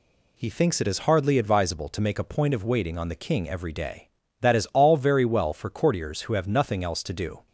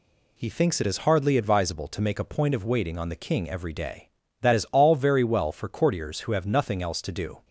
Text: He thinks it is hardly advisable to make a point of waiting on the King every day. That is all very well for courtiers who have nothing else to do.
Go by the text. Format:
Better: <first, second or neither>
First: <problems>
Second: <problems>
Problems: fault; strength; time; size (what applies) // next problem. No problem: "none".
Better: neither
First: none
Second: none